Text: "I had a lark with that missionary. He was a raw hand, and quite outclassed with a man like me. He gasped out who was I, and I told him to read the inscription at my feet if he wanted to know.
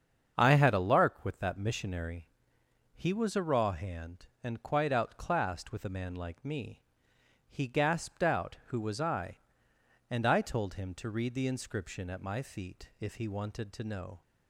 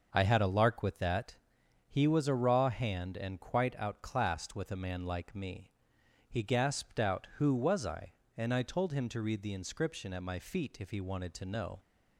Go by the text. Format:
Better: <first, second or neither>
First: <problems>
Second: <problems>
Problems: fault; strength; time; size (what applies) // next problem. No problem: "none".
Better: first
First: starts louder than the rest; strong; until 1.3 s; 7 dB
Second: starts louder than the rest; noticeable; until 1.1 s; 6 dB // skips "missionary"; at 1.6 s